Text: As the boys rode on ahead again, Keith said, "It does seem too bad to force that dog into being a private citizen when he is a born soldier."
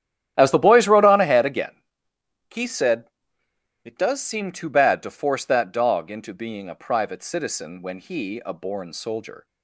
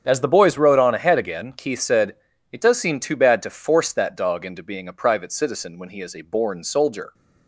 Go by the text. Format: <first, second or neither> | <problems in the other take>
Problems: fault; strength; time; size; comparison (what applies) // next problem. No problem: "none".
second | starts louder than the rest; strong; until 1.3 s; 12 dB; strong in the second // skips "is"; at 8.4 s